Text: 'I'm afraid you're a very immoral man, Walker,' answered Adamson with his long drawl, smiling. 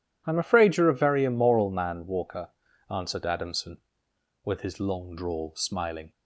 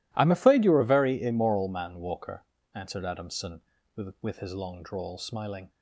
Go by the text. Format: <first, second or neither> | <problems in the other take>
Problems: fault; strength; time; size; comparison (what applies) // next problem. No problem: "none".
first | says "with" twice; at 4.1 s